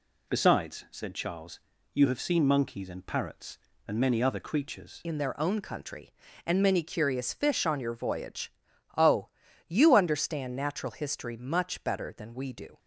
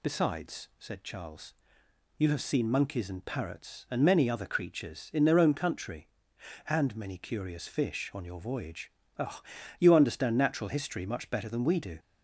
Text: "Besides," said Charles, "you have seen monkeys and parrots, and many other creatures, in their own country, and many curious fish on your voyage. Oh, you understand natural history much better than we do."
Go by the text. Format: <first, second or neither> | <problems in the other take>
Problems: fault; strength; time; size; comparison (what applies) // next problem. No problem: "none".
second | changes voice at "in"; from 5.0 s on; 7.7 s long